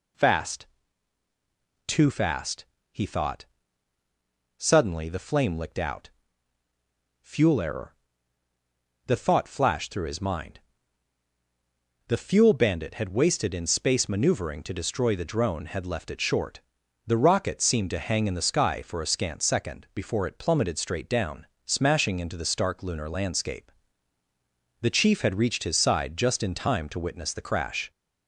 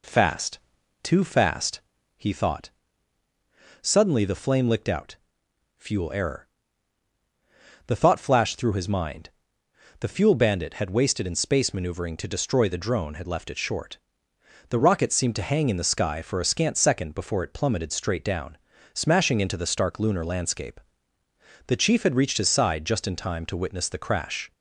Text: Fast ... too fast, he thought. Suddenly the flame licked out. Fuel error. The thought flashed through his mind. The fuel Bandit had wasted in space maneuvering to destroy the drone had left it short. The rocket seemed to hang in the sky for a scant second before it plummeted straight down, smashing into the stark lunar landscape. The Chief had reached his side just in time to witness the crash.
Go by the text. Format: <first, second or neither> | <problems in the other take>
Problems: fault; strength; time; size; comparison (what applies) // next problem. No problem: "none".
second | gets louder; slight; throughout; 2 dB